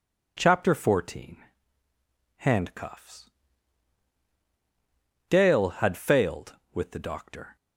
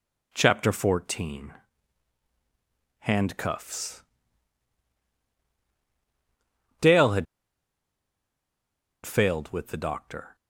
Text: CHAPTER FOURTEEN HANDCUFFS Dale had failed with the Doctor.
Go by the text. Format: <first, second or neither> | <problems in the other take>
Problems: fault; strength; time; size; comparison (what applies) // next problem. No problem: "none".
first | pauses between "FOURTEEN" and "HANDCUFFS"; strong; at 1.5 s; 1.4 s long; also in the first // pauses between "HANDCUFFS" and "Dale"; strong; at 4.0 s; 2.7 s long; strong in the first // pauses between "had" and "failed"; strong; at 7.2 s; 1.7 s long